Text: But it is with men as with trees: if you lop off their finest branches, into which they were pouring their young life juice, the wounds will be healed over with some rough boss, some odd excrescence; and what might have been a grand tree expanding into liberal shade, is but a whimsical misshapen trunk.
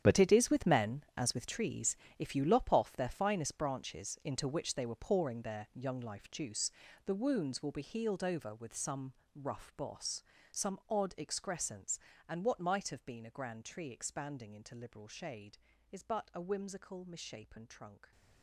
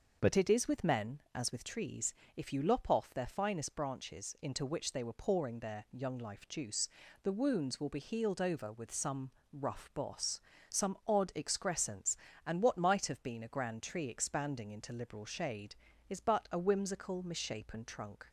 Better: second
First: gets quieter; strong; throughout; 14 dB // starts louder than the rest; strong; until 1.0 s; 9.5 dB // pauses between "some" and "rough"; slight; at 9.1 s; 0.24 s long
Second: starts louder than the rest; noticeable; until 1.2 s; 6 dB // pauses between "some" and "rough"; slight; at 9.2 s; 0.24 s long

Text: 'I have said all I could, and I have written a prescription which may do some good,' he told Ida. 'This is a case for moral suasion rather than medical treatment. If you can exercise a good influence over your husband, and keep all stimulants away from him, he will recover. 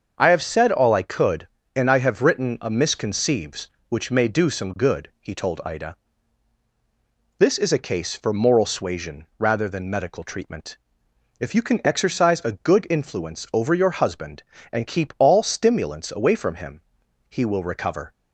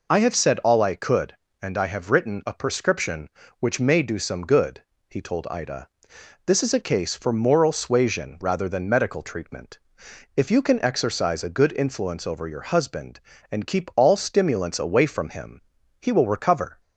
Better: second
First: starts louder than the rest; until 1.1 s; 6.5 dB // says "misconceives" for "prescription"; at 2.6 s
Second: none

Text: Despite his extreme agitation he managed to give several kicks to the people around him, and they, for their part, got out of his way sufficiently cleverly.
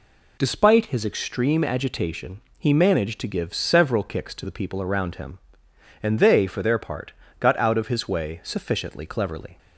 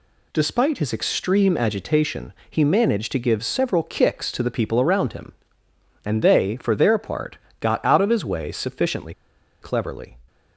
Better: first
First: pauses between "agitation" and "he"; slight; at 2.3 s; 0.18 s long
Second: pauses between "agitation" and "he"; slight; at 2.3 s; 0.16 s long // pauses between "sufficiently" and "cleverly"; noticeable; at 9.1 s; 0.48 s long

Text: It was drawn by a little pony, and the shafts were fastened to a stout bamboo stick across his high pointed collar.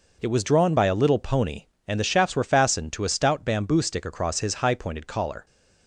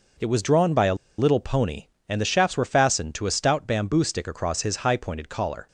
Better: first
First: none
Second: pauses between "a" and "little"; slight; at 0.9 s; 0.22 s long

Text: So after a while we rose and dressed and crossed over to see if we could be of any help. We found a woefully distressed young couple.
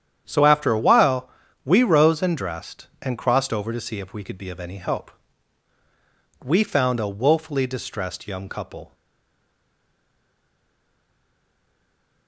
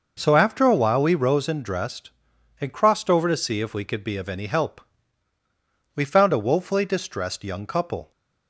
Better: second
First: starts louder than the rest; strong; until 1.2 s; 9 dB // pauses between "while" and "we"; slight; at 1.2 s; 0.34 s long // stays silent after the last word; strong; from 8.9 s on; 3.3 s long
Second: none

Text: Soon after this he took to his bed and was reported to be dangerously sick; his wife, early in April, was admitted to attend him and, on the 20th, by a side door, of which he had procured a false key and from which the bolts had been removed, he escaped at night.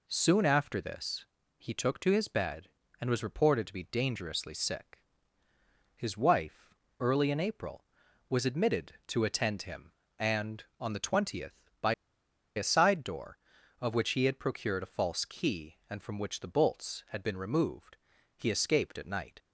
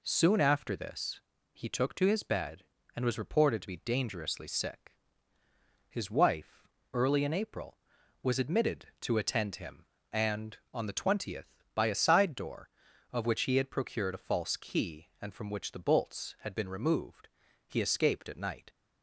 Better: second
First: pauses between "this" and "he"; slight; at 1.2 s; 0.34 s long // pauses between "by" and "a"; noticeable; at 11.9 s; 0.63 s long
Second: pauses between "this" and "he"; slight; at 1.1 s; 0.34 s long

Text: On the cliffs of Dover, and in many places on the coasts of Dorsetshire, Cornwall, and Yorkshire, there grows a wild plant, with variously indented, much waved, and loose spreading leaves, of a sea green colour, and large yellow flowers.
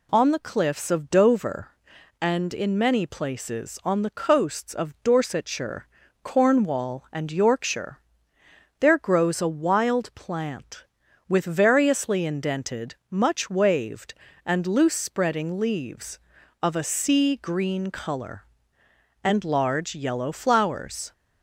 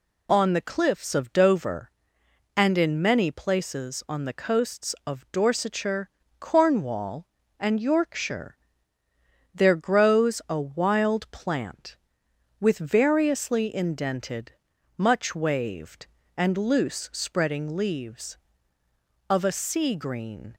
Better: first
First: none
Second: stops before "colour and large yellow flowers"; at 20.5 s

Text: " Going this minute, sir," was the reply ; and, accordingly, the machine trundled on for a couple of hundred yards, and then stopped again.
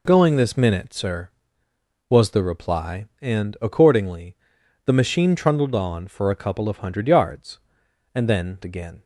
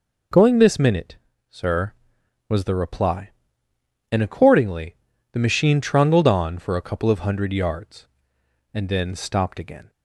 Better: second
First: skips "stopped"; at 8.6 s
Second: none

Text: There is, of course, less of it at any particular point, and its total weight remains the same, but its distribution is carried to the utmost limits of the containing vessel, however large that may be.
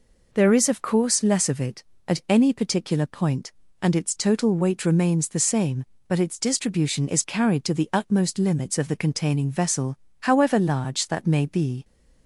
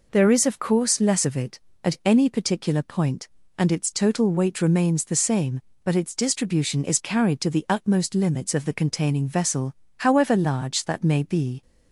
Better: neither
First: none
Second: none

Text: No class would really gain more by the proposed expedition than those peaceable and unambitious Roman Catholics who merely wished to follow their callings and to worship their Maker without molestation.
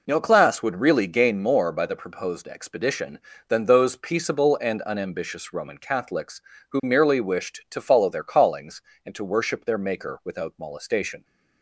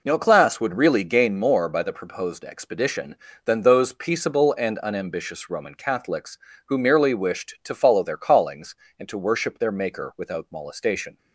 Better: neither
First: none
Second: none

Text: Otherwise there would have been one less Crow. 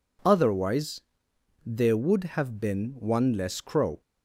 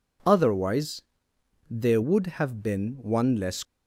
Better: first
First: pauses between "Otherwise" and "there"; noticeable; at 0.9 s; 0.64 s long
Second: pauses between "Otherwise" and "there"; noticeable; at 1.0 s; 0.68 s long // stops before "Crow"; at 3.6 s

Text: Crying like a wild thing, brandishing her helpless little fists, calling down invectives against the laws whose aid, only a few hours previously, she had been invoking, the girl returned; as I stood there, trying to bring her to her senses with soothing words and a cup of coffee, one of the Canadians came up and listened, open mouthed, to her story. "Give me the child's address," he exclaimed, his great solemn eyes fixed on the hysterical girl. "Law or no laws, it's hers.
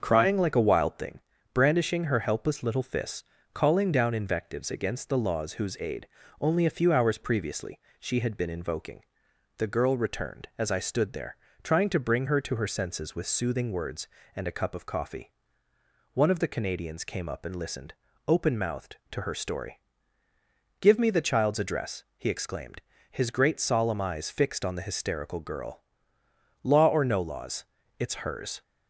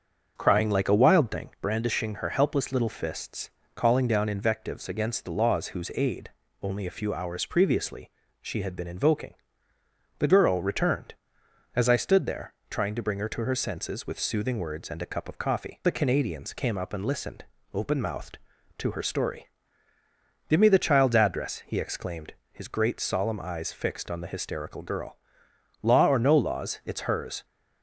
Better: first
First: starts louder than the rest; until 1.0 s; 6.5 dB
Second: starts louder than the rest; until 1.3 s; 7 dB // skips "one of"; at 15.8 s

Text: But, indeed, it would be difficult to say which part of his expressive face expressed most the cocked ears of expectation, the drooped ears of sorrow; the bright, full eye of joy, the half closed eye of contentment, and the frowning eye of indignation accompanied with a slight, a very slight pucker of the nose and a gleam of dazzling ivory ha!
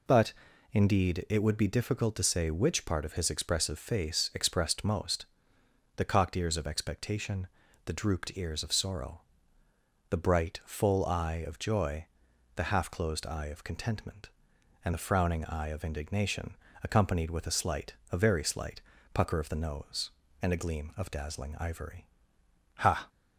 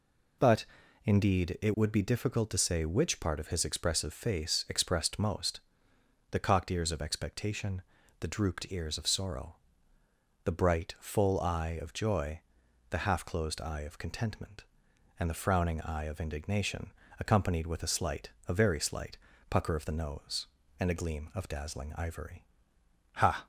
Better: neither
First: pauses between "most" and "the"; noticeable; at 5.2 s; 0.72 s long // pauses between "indignation" and "accompanied"; slight; at 16.5 s; 0.30 s long // pauses between "slight" and "pucker"; slight; at 18.8 s; 0.32 s long // pauses between "ivory" and "ha"; noticeable; at 22.0 s; 0.74 s long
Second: pauses between "most" and "the"; noticeable; at 5.5 s; 0.72 s long // pauses between "indignation" and "accompanied"; slight; at 16.8 s; 0.30 s long // pauses between "slight" and "pucker"; slight; at 19.1 s; 0.32 s long // pauses between "ivory" and "ha"; noticeable; at 22.4 s; 0.74 s long

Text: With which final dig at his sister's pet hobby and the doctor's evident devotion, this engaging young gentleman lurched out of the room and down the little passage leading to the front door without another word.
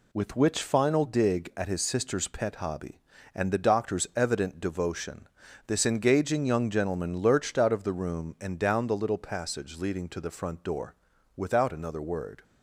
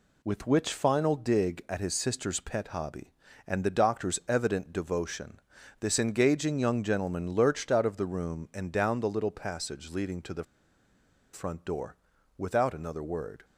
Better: first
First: pauses between "door" and "without"; at 10.9 s; 0.40 s long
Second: pauses between "the" and "front"; noticeable; at 10.4 s; 0.89 s long // pauses between "door" and "without"; at 11.9 s; 0.40 s long

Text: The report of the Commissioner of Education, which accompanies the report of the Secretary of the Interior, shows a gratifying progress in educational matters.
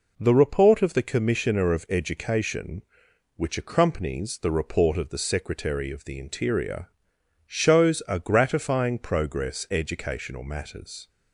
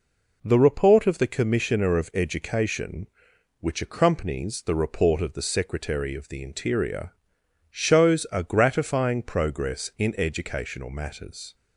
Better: second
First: skips "in"; at 9.6 s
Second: none

